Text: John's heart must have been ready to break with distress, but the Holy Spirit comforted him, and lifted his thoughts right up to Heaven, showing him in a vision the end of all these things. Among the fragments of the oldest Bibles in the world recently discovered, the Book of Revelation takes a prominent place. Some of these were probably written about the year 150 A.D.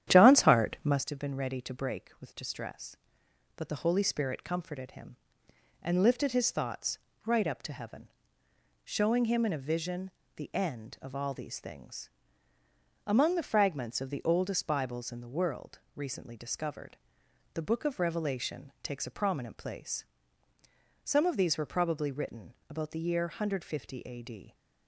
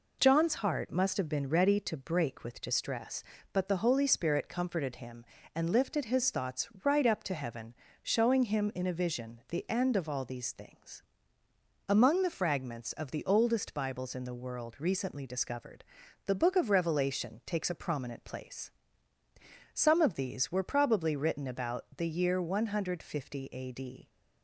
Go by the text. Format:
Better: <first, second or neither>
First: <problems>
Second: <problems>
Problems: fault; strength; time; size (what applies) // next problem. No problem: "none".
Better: second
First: starts louder than the rest; strong; until 1.0 s; 10.5 dB // pauses between "thoughts" and "right"; slight; at 6.9 s; 0.30 s long // pauses between "vision" and "the"; slight; at 10.0 s; 0.28 s long // pauses between "world" and "recently"; slight; at 15.7 s; 0.16 s long // pauses between "written" and "about"; slight; at 22.5 s; 0.16 s long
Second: pauses between "thoughts" and "right"; slight; at 6.6 s; 0.16 s long